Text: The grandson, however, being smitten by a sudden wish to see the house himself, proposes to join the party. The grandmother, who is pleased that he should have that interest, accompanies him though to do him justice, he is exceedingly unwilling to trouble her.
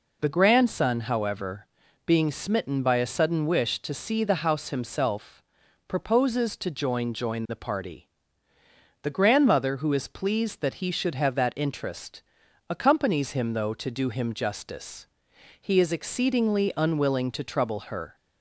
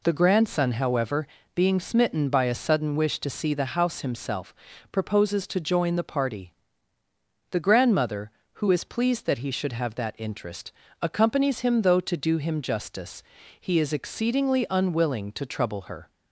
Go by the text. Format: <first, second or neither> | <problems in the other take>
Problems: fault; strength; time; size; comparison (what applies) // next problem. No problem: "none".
second | says "join" twice; at 7.1 s